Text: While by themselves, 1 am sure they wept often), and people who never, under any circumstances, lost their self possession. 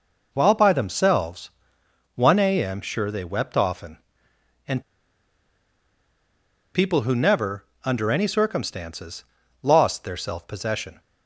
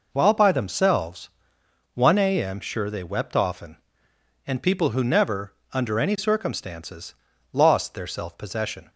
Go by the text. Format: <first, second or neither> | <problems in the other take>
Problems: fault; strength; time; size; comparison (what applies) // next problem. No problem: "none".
second | pauses between "and" and "people"; strong; at 4.8 s; 1.9 s long